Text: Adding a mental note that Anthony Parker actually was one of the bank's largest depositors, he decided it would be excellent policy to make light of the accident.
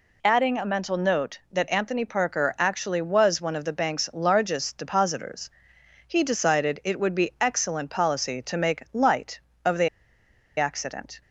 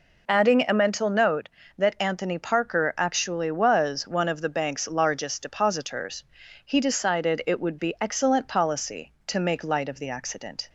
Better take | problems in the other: second | pauses between "the" and "accident"; noticeable; at 9.8 s; 0.69 s long

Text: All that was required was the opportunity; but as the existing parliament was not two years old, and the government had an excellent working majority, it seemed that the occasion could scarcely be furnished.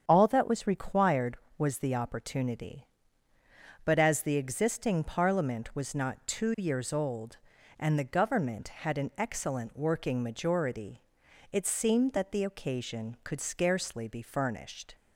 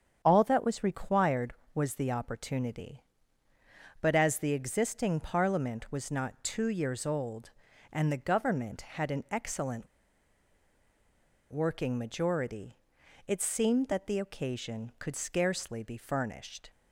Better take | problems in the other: first | starts louder than the rest; strong; until 1.2 s; 8 dB; strong in the first // pauses between "excellent" and "working"; strong; at 9.8 s; 1.6 s long

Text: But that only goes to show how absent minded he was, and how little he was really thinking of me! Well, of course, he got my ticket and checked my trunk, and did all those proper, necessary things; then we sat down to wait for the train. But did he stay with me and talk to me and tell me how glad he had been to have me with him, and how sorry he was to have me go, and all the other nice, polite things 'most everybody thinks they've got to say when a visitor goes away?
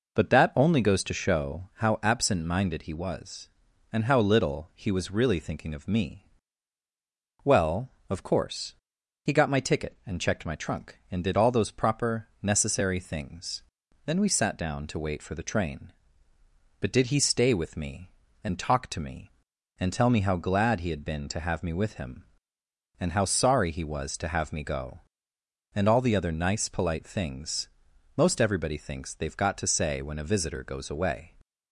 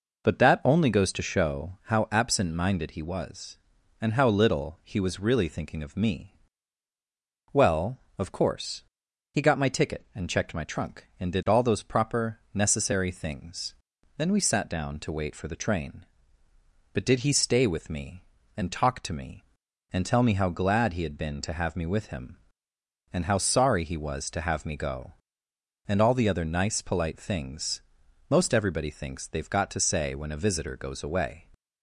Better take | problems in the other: neither | pauses between "things" and "most"; noticeable; the same in both

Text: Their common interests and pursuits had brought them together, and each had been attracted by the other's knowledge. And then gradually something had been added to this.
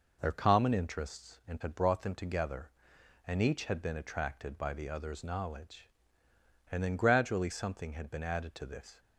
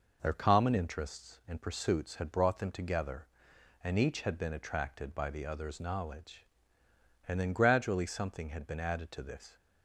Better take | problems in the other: second | skips "pursuits"; at 1.6 s

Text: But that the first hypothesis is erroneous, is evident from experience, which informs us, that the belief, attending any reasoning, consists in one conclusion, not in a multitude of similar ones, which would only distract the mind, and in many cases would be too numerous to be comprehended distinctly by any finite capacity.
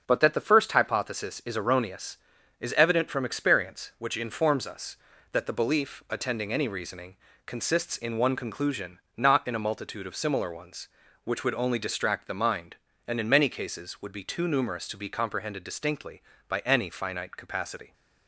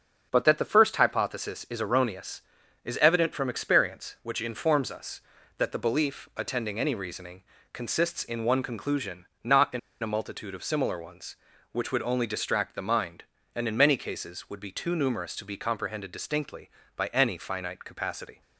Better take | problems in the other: first | starts louder than the rest; until 1.3 s; 7 dB; also in the first // pauses between "in" and "a"; slight; at 9.7 s; 0.22 s long

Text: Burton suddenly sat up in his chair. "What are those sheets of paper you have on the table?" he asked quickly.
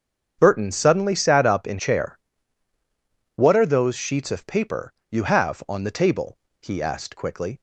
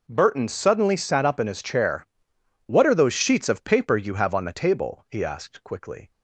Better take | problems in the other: second | starts louder than the rest; strong; until 1.4 s; 7.5 dB // skips "his"; at 1.7 s // pauses between "paper" and "you"; slight; at 4.9 s; 0.20 s long

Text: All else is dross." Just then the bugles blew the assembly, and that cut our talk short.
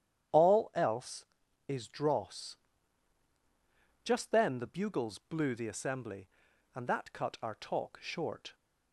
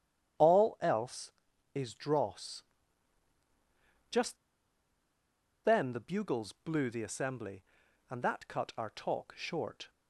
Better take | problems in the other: first | starts louder than the rest; strong; until 1.8 s; 9.5 dB; strong in the first // pauses between "Just" and "then"; strong; at 4.3 s; 1.2 s long

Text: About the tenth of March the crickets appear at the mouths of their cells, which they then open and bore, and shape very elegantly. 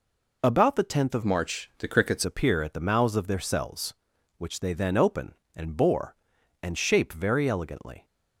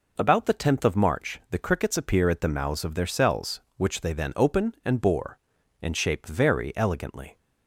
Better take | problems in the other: second | changes voice from "March" to "crickets"; from 1.2 to 2.2 s; 1.0 s long

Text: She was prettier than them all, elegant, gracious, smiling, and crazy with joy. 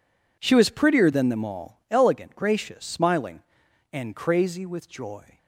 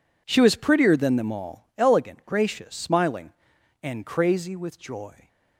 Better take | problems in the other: neither | none

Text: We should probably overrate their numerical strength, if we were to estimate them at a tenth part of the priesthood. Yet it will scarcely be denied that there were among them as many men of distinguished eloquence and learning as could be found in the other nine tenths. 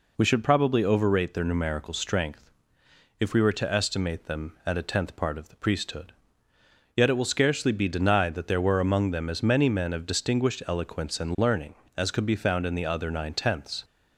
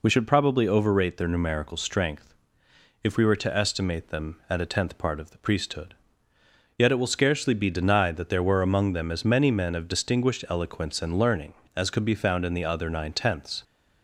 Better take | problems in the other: neither | none

